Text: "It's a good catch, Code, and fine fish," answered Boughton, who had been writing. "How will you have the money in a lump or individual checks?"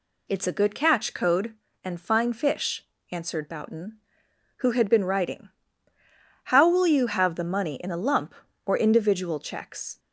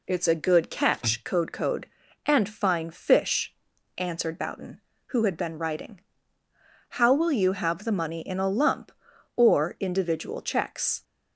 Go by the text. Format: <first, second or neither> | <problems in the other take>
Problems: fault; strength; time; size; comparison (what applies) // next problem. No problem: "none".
first | says "Code" twice; at 1.5 s